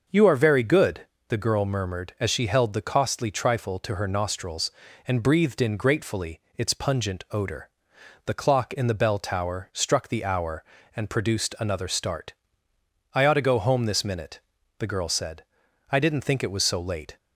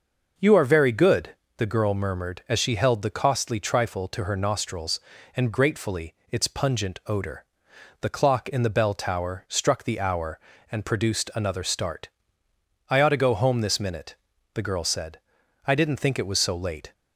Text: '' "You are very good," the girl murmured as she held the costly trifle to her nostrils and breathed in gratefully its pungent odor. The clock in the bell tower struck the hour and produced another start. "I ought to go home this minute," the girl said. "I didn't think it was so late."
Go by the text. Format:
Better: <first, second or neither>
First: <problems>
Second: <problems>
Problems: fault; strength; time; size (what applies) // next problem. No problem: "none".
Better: first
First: pauses between "gratefully" and "its"; slight; at 6.4 s; 0.16 s long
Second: skips "breathed in"; at 5.5 s // pauses between "gratefully" and "its"; slight; at 6.1 s; 0.16 s long